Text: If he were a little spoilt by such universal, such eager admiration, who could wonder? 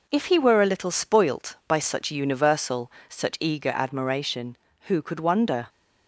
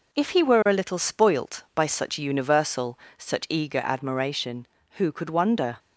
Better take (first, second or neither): neither